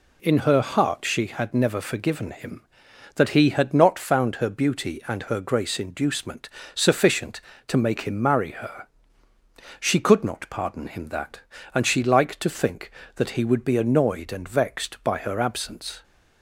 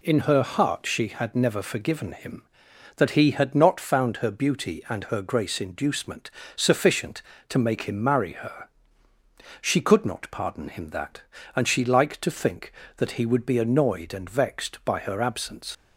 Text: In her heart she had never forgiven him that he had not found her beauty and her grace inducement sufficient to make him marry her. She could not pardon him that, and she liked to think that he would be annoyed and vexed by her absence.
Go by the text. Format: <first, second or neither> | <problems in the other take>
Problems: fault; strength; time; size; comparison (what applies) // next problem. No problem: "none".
first | pauses between "inducement" and "sufficient"; slight; at 6.3 s; 0.26 s long; slight in the first // leaves "absence" unfinished; at 15.7 s; 90 ms